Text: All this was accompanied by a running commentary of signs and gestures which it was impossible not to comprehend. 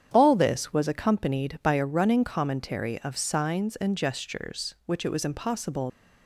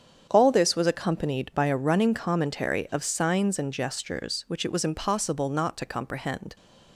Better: second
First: starts louder than the rest; strong; until 1.1 s; 8.5 dB // stops before "not to comprehend"; at 5.8 s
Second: starts louder than the rest; strong; until 1.3 s; 8 dB

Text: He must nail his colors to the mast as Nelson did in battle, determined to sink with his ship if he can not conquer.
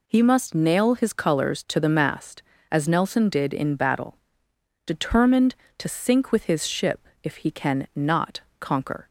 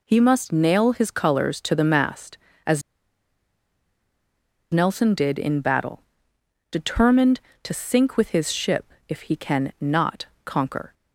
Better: first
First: pauses between "ship" and "if"; slight; at 7.0 s; 0.16 s long // pauses between "not" and "conquer"; slight; at 8.4 s; 0.18 s long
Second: pauses between "as" and "Nelson"; strong; at 2.8 s; 1.9 s long // pauses between "ship" and "if"; slight; at 8.9 s; 0.16 s long // pauses between "not" and "conquer"; slight; at 10.2 s; 0.18 s long

